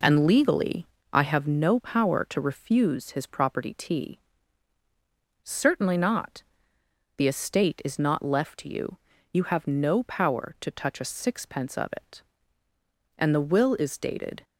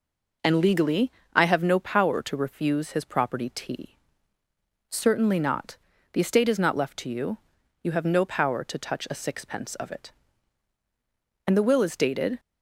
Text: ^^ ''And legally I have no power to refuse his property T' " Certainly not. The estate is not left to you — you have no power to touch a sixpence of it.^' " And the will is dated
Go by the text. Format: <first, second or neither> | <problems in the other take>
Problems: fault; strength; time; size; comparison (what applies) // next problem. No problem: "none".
neither | pauses between "legally" and "I"; slight; the same in both